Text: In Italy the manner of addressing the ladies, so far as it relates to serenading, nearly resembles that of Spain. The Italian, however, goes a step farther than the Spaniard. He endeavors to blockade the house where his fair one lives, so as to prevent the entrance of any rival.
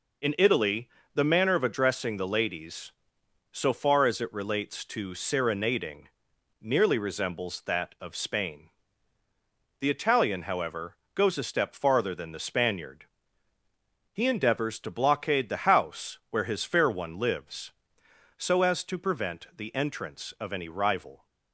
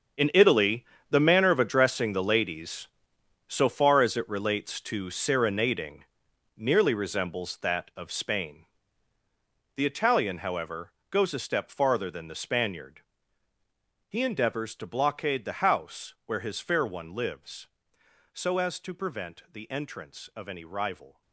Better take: first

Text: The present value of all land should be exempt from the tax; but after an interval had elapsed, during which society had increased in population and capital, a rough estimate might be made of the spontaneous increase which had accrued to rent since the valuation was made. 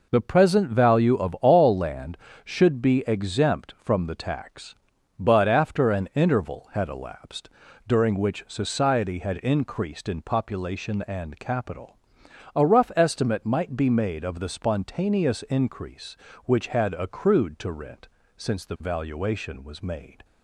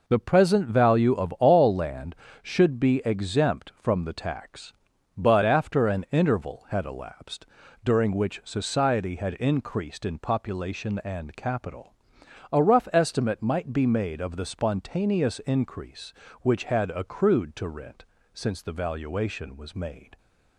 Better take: neither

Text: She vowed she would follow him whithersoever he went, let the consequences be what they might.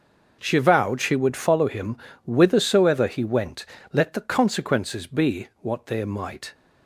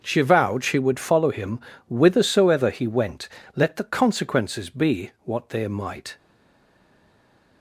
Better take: first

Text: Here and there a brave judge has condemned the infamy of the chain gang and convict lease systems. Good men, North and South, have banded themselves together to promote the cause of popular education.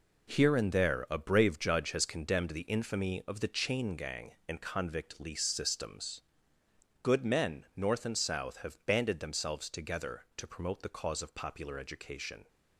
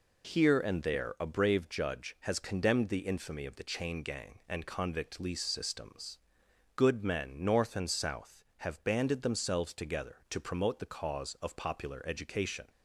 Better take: second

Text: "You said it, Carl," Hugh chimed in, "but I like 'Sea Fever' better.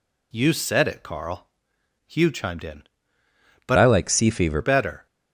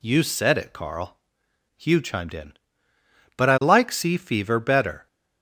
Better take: second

